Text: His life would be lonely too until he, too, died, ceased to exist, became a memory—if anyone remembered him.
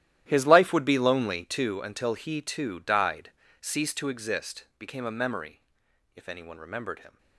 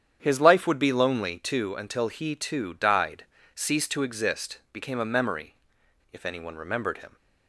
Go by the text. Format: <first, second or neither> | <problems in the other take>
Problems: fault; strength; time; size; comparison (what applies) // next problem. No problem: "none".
second | gets quieter; strong; throughout; 15.5 dB // starts louder than the rest; strong; until 1.2 s; 13 dB; strong in the second